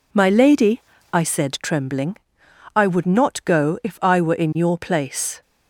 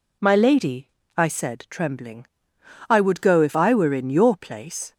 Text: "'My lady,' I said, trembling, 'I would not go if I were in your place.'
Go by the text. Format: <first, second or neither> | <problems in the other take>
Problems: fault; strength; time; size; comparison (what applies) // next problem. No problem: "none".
first | skips "not"; at 3.2 s